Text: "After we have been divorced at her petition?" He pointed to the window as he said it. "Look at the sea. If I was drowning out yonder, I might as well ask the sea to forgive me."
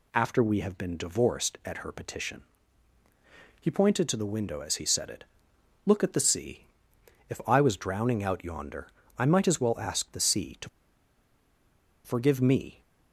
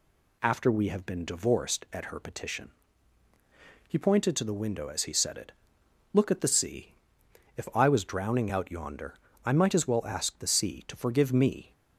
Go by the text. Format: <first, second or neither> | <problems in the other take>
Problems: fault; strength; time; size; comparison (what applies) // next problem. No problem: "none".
second | pauses between "to" and "forgive"; strong; at 10.6 s; 1.3 s long